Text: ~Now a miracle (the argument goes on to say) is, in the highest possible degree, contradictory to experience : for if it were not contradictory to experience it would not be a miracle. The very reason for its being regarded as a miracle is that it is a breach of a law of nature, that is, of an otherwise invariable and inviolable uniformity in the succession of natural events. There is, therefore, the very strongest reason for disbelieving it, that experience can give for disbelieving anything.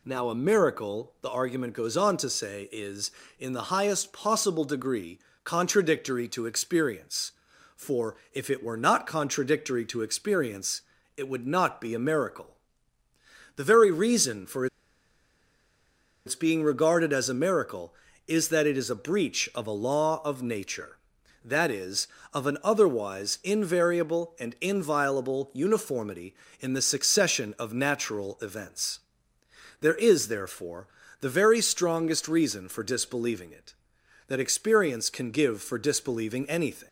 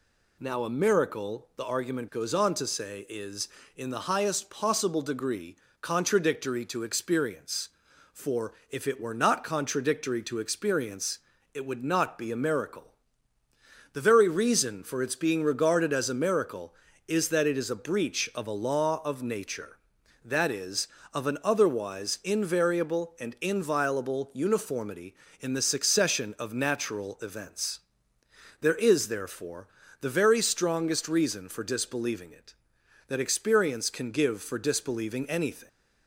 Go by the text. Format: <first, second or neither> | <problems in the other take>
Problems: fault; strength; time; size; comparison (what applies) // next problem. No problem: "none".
second | pauses between "for" and "if"; slight; at 8.1 s; 0.16 s long; slight in the second // pauses between "experience" and "it"; slight; at 10.8 s; 0.34 s long; slight in the second // pauses between "for" and "its"; strong; at 14.6 s; 1.5 s long